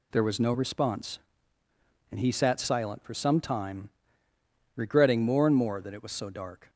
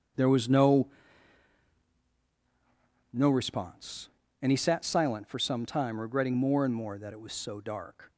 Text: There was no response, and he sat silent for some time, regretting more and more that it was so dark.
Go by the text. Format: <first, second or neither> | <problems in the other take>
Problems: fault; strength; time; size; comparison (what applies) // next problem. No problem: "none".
first | starts louder than the rest; strong; until 3.4 s; 7.5 dB // says "no" twice; at 3.1 s